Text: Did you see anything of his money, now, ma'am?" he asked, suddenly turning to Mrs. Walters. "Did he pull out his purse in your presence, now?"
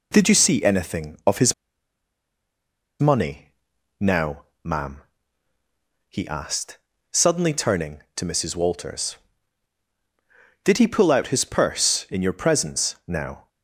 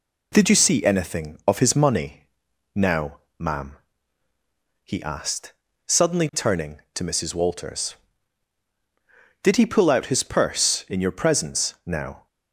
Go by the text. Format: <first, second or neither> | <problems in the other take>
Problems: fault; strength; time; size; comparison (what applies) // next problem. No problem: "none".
second | pauses between "his" and "money"; strong; at 1.5 s; 1.4 s long